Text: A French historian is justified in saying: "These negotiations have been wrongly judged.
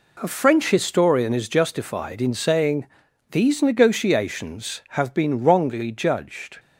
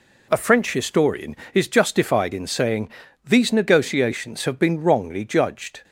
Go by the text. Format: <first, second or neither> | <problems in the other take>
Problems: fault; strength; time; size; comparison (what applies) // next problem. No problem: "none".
neither | none